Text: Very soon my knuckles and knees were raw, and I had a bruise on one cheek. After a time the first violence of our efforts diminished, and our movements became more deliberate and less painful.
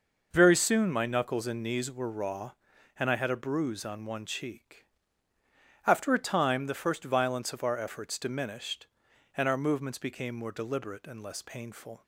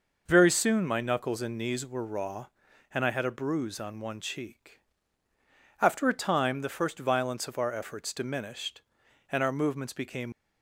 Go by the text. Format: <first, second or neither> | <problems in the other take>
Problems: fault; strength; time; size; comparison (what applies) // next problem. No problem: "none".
first | stops before "more deliberate and less painful"; at 10.3 s